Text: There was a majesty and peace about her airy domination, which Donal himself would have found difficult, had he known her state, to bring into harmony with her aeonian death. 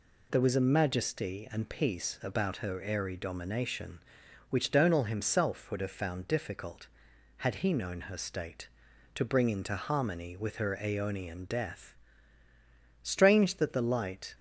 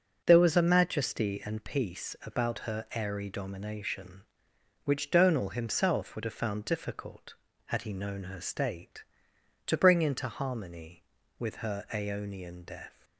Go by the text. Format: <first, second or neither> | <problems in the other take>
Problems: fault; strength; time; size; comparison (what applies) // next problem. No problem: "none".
second | goes on to say "Strange that the light"; noticeable; from 13.1 s on; 1.1 s long